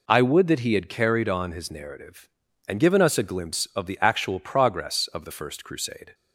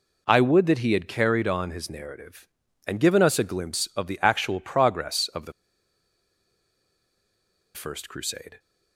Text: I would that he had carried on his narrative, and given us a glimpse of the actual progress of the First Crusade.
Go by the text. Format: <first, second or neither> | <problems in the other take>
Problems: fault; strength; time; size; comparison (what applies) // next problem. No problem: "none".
first | pauses between "the" and "First"; strong; at 5.5 s; 2.2 s long